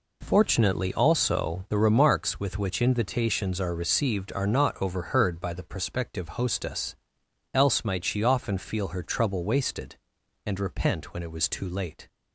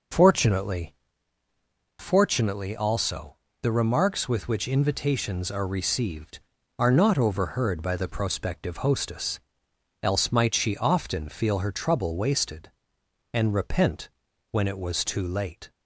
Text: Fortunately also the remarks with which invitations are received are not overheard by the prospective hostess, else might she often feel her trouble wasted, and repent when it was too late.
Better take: first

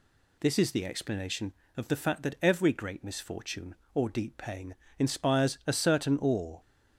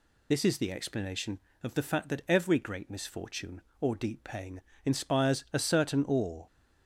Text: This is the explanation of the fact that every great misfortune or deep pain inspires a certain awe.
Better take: first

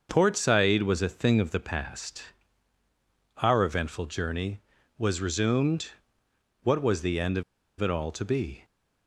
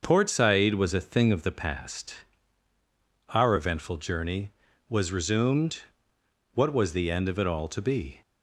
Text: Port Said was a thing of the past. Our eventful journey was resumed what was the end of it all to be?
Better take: second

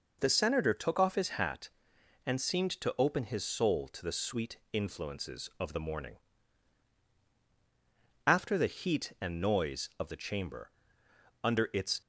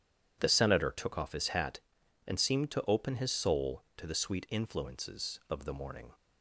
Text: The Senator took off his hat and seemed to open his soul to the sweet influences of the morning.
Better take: second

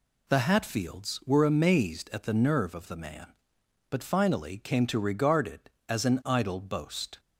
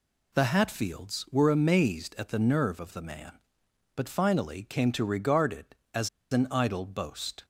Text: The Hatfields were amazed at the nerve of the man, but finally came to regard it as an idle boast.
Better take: first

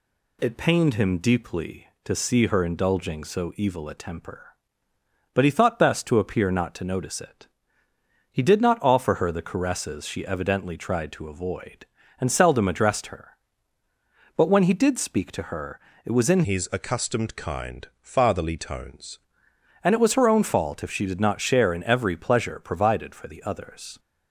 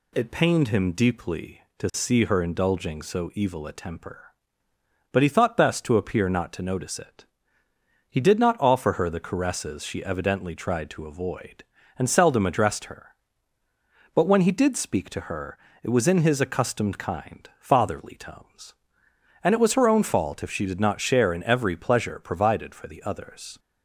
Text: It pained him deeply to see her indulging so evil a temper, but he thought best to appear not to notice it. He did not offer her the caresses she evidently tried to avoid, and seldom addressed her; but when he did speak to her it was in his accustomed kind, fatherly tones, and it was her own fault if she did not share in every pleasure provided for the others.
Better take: second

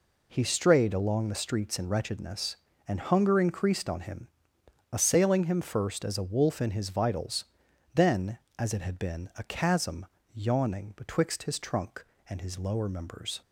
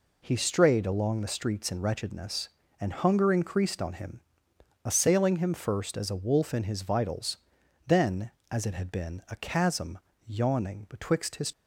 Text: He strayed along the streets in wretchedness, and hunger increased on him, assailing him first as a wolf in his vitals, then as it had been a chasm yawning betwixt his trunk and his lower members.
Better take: first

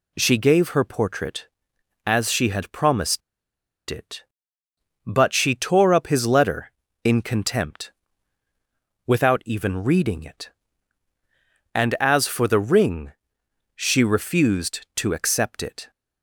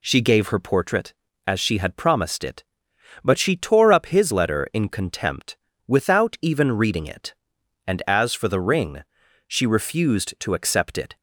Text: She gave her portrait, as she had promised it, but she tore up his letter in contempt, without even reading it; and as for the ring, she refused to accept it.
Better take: second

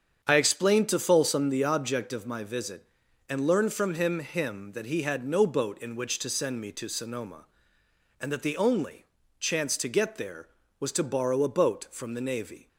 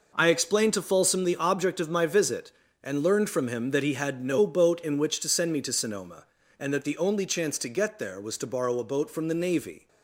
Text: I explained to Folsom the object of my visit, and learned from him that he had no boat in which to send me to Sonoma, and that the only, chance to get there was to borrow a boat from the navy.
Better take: second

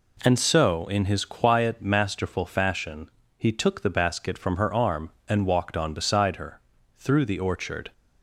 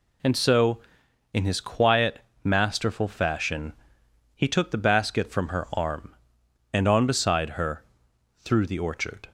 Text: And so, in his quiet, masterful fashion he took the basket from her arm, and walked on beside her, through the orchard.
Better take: first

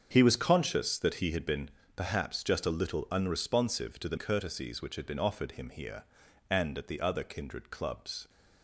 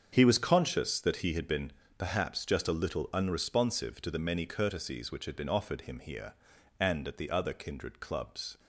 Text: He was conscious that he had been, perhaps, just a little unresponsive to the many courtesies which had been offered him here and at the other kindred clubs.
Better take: second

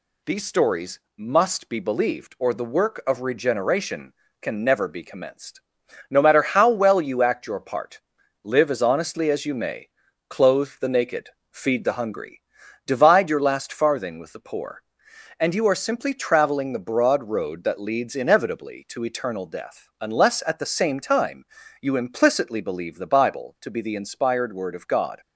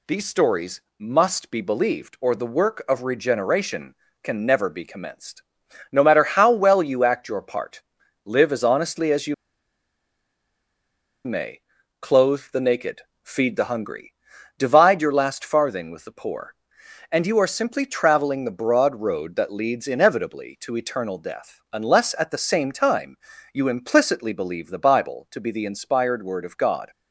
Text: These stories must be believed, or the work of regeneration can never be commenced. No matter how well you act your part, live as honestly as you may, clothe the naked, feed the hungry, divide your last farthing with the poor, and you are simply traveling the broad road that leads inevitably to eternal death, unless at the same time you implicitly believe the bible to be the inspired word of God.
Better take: first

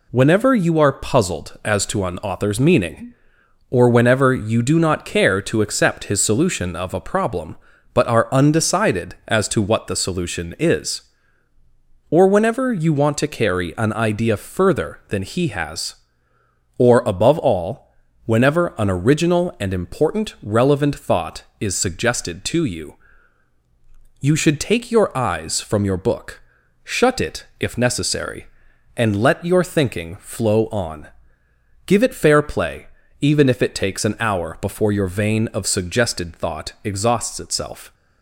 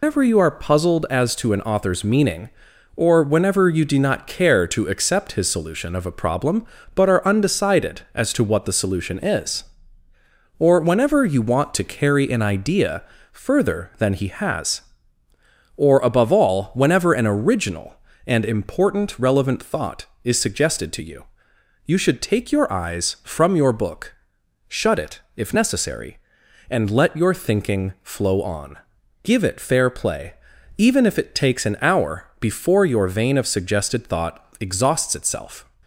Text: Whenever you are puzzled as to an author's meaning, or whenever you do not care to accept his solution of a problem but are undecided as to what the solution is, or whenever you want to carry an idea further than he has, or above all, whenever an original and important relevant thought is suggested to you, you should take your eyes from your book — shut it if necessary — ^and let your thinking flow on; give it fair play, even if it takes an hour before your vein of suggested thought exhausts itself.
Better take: first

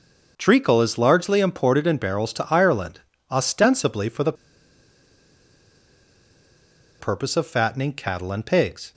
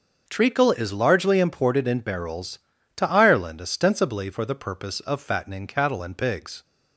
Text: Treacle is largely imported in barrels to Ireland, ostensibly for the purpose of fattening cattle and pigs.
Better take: second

